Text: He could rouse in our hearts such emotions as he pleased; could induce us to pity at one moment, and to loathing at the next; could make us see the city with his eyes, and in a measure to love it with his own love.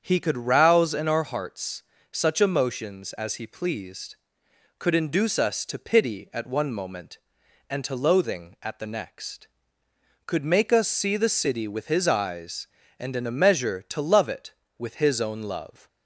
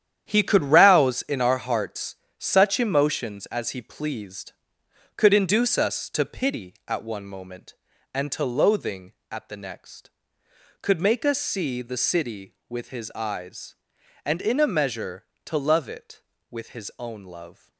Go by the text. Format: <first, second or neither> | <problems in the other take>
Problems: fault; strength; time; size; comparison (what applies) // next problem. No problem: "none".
first | gets quieter; strong; throughout; 9.5 dB // starts louder than the rest; strong; until 1.3 s; 9.5 dB; strong in the first // pauses between "hearts" and "such"; slight; at 2.1 s; 0.22 s long; slight in the first